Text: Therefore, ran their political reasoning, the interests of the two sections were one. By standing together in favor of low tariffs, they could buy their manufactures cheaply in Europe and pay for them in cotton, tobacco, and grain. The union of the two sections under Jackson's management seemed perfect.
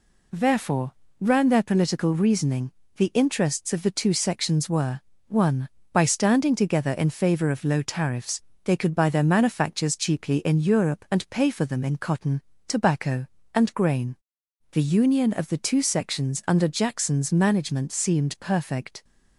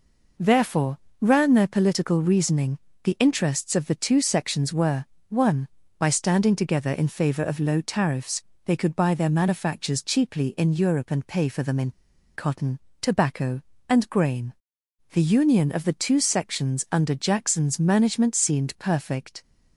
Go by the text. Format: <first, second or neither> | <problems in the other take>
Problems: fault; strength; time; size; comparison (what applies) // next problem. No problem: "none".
first | pauses between "were" and "one"; slight; at 5.0 s; 0.24 s long; slight in the first // pauses between "in" and "cotton"; at 11.9 s; 0.44 s long